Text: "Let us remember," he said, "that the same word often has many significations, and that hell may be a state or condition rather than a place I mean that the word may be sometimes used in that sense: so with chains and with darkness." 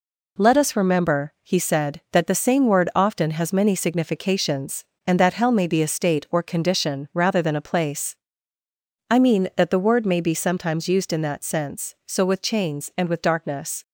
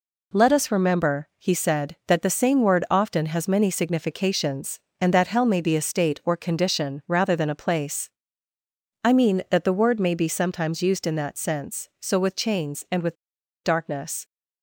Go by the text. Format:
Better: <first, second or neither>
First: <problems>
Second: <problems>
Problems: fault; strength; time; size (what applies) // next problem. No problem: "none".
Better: first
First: pauses between "place" and "I"; noticeable; at 8.1 s; 0.96 s long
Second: pauses between "place" and "I"; noticeable; at 8.0 s; 0.96 s long // pauses between "with" and "darkness"; noticeable; at 13.1 s; 0.49 s long